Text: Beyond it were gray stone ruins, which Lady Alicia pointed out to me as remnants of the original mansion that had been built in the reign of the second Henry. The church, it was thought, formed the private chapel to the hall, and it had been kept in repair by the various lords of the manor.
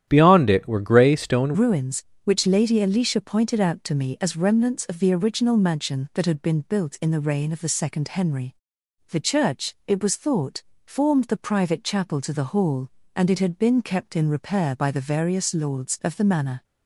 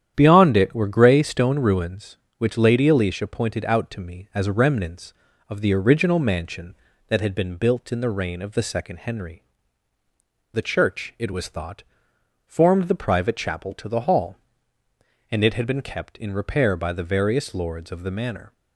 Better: second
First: starts louder than the rest; strong; until 1.0 s; 10.5 dB // changes voice at "ruins"; from 1.5 s on; 15.1 s long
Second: starts louder than the rest; strong; until 1.1 s; 10 dB

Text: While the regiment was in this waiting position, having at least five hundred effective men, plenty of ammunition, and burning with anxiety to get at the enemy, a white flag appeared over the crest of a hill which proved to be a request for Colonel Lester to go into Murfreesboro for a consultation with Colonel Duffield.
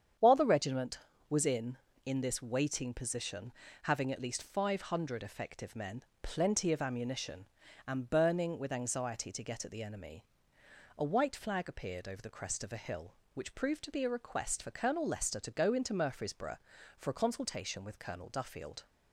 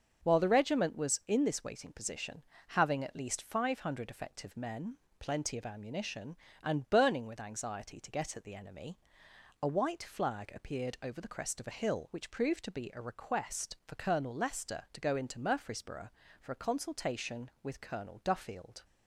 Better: second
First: starts louder than the rest; strong; until 1.5 s; 8.5 dB // says "in" twice; at 2.0 s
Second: starts louder than the rest; until 1.3 s; 7 dB

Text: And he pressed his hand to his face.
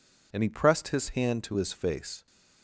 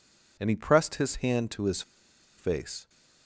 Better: first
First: none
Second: pauses between "his" and "face"; noticeable; at 1.8 s; 0.56 s long

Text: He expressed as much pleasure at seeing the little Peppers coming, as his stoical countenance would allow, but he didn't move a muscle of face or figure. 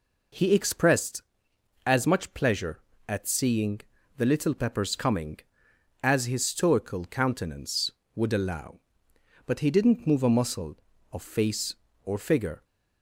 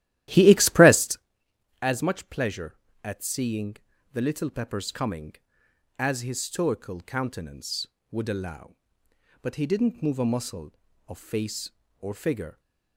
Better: first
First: pauses between "seeing" and "the"; slight; at 3.8 s; 0.36 s long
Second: starts louder than the rest; strong; until 1.3 s; 14 dB // pauses between "seeing" and "the"; slight; at 3.7 s; 0.36 s long

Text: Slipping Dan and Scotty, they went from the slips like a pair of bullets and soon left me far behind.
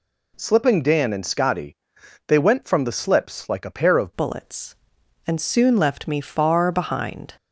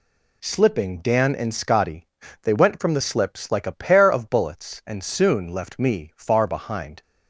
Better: second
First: changes voice at "bullets"; from 4.1 s on; 3.2 s long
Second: none

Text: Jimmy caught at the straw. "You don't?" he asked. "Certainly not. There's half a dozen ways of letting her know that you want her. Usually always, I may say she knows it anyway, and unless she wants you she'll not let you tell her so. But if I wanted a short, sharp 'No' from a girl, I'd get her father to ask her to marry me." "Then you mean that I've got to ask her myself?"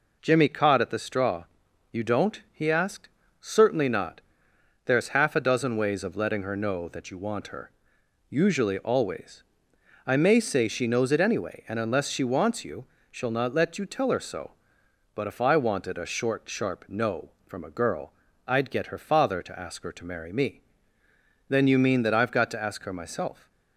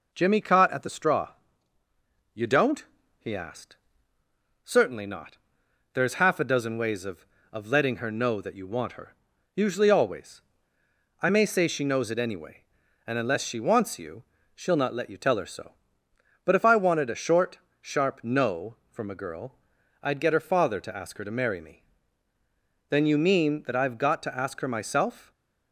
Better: first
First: pauses between "you" and "she'll"; slight; at 12.8 s; 0.24 s long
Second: says "of" twice; at 7.5 s // pauses between "you" and "she'll"; slight; at 14.2 s; 0.32 s long

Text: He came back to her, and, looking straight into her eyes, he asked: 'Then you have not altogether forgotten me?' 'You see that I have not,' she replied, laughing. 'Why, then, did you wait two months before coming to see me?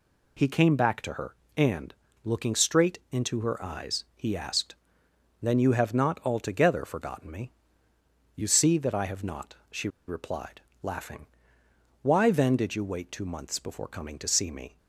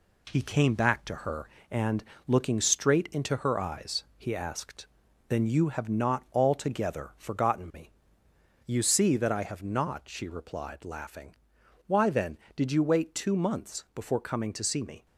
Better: second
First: pauses between "she" and "replied"; slight; at 9.8 s; 0.20 s long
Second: none

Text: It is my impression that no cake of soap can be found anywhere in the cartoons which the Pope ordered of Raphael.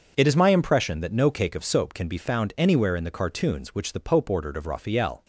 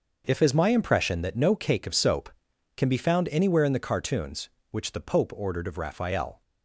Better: first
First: starts louder than the rest; until 1.1 s; 6.5 dB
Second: starts louder than the rest; noticeable; until 1.2 s; 6 dB // says "If" for "It"; at 0.2 s

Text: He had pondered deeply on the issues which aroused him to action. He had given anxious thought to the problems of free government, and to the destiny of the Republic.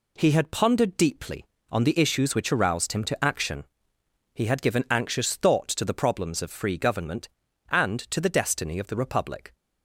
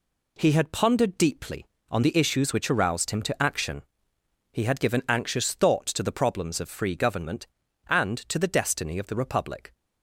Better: neither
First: none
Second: none

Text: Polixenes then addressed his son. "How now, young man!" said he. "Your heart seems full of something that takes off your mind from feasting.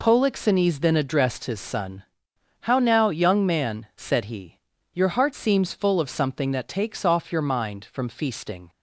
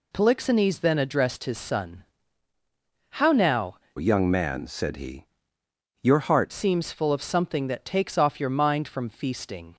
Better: first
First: none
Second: changes voice from "young" to "heart"; from 3.9 to 6.5 s; 2.6 s long

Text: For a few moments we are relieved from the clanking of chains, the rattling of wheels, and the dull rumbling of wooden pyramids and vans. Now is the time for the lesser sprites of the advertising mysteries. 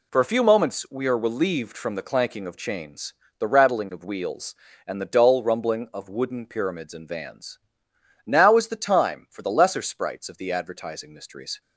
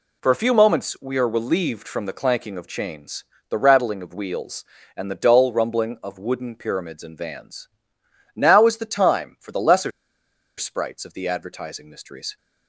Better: first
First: none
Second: pauses between "lesser" and "sprites"; noticeable; at 9.9 s; 0.67 s long

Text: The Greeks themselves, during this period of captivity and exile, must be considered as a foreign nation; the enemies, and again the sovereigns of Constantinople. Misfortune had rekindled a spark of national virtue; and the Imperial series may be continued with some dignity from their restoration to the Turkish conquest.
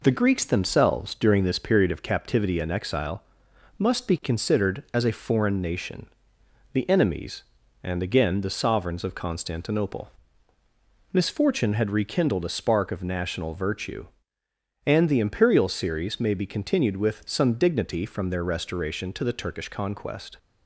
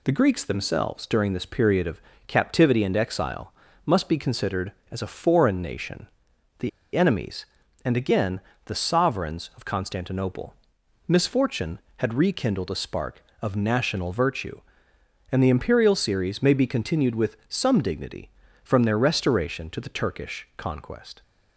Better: first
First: none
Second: pauses between "of" and "captivity"; slight; at 2.0 s; 0.26 s long // pauses between "the" and "enemies"; slight; at 6.6 s; 0.26 s long // pauses between "again" and "the"; slight; at 8.4 s; 0.26 s long

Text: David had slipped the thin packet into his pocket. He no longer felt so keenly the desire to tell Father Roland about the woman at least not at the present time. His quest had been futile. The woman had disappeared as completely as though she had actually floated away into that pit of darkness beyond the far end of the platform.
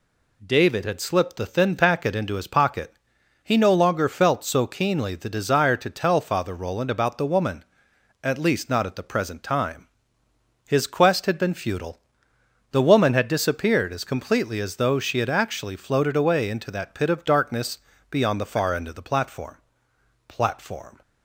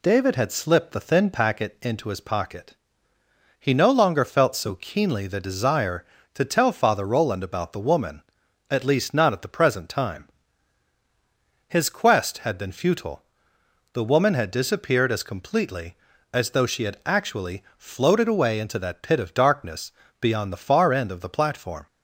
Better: second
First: pauses between "darkness" and "beyond"; slight; at 17.7 s; 0.32 s long // says "platform" twice; at 20.2 s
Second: pauses between "darkness" and "beyond"; slight; at 19.9 s; 0.30 s long

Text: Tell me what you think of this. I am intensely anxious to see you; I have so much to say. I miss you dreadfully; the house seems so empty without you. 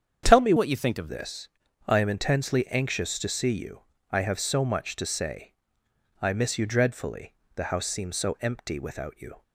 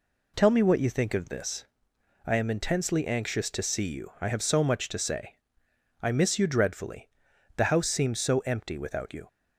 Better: second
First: starts louder than the rest; strong; until 1.2 s; 8 dB // changes voice from "what" to "of"; from 0.5 to 1.0 s; 0.5 s long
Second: none

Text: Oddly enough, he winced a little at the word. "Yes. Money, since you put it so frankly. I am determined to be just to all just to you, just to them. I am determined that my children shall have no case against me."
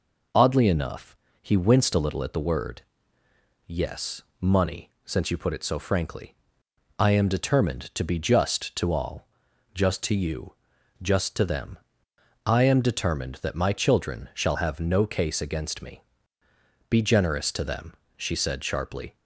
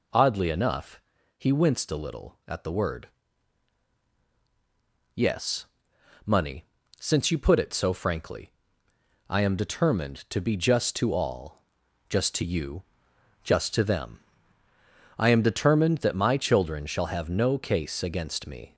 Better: second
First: pauses between "all" and "just"; noticeable; at 9.2 s; 0.46 s long // goes on to say "Be generous to them she said sharply"; strong; from 16.8 s on; 2.2 s long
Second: pauses between "all" and "just"; noticeable; at 11.5 s; 0.50 s long

